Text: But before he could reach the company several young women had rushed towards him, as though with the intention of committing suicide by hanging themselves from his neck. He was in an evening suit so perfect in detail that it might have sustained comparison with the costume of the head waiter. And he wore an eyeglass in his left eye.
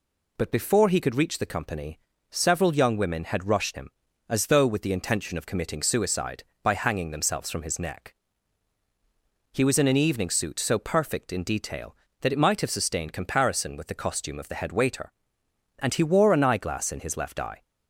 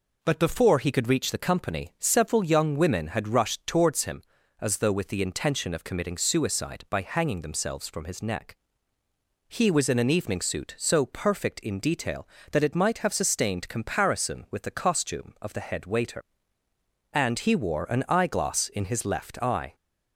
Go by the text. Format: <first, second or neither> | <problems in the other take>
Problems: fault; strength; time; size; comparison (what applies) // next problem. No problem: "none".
second | pauses between "company" and "several"; slight; at 1.9 s; 0.32 s long // skips "towards"; at 3.7 s